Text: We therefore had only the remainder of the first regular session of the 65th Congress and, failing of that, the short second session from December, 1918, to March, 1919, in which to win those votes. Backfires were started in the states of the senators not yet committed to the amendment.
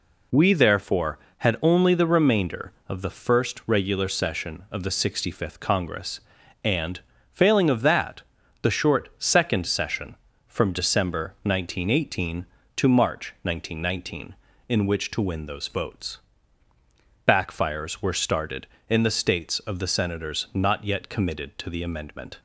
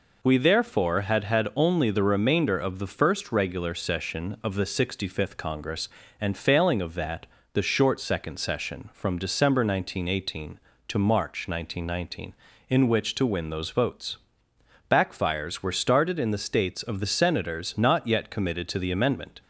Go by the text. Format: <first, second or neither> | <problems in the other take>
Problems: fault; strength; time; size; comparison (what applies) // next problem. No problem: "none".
first | says "had" twice; at 1.2 s